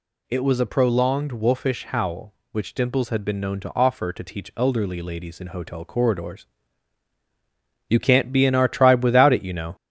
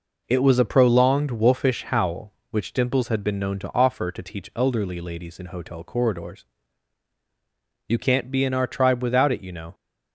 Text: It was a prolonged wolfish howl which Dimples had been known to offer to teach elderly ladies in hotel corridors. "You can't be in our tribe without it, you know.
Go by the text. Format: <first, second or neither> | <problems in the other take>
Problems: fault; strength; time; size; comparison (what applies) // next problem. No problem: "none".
second | gets louder; noticeable; throughout; 4 dB